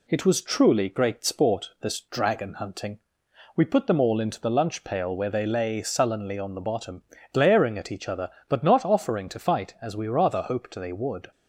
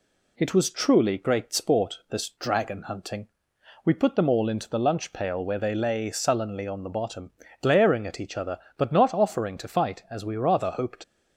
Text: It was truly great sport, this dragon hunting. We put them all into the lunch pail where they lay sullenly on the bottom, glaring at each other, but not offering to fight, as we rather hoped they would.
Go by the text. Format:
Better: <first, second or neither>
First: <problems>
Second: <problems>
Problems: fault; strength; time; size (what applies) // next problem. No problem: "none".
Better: first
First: none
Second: stops before "they would"; at 11.0 s